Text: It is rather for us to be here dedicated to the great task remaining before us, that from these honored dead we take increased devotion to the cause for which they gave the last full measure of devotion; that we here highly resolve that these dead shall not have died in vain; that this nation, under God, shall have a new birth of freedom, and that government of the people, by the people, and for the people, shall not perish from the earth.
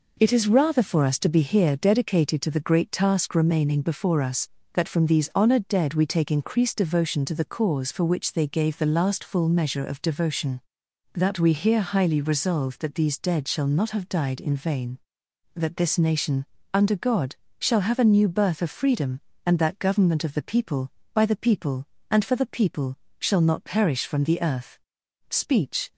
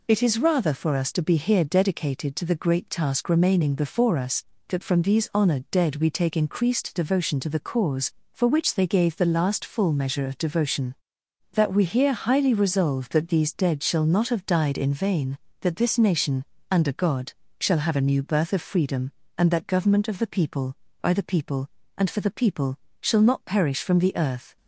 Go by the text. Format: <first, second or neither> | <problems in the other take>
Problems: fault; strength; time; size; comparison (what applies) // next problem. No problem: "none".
second | goes on to say "Speech"; noticeable; from 25.3 s on; 0.62 s long